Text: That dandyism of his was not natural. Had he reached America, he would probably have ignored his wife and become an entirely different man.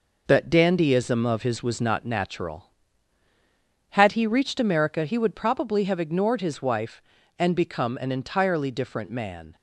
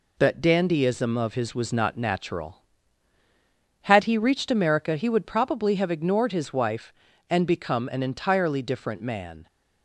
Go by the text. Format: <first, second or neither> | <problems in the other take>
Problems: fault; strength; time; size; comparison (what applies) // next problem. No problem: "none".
second | starts louder than the rest; noticeable; until 1.9 s; 5 dB